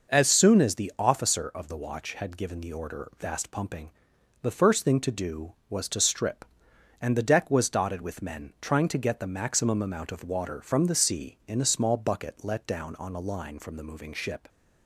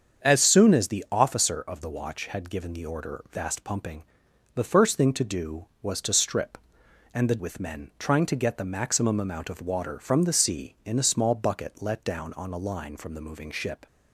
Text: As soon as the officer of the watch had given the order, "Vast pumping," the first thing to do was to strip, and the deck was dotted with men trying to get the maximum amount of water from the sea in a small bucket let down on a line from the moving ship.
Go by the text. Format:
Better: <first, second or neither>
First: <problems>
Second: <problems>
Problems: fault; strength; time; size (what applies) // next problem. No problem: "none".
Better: first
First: none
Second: starts louder than the rest; strong; until 1.3 s; 7.5 dB // skips "deck was dotted"; at 7.3 s